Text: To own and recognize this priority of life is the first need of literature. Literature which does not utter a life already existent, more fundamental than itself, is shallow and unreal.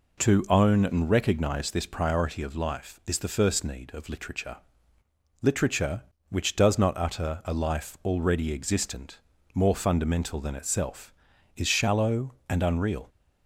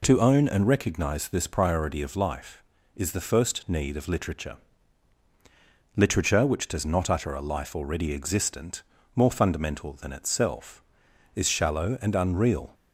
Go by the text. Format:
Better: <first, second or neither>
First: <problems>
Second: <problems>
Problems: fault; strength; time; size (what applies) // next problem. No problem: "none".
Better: neither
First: none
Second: none